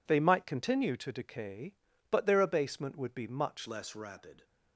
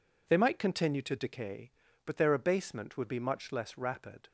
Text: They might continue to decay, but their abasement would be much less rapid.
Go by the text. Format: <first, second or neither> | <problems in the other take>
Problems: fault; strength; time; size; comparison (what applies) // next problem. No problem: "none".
second | changes voice at "less"; from 3.6 s on; 0.8 s long